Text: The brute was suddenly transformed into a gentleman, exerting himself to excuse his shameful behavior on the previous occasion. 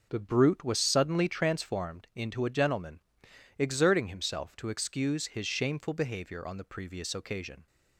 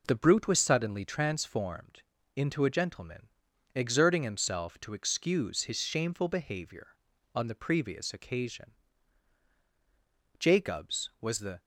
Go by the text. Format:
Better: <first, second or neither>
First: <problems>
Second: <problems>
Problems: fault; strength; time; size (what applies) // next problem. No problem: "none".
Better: first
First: none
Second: pauses between "transformed" and "into"; slight; at 2.0 s; 0.34 s long // goes on to say "Jacobs was the"; noticeable; from 10.3 s on; 1.2 s long